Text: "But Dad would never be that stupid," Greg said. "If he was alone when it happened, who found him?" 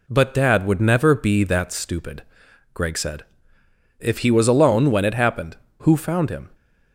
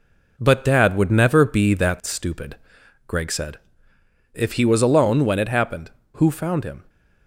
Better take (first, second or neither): first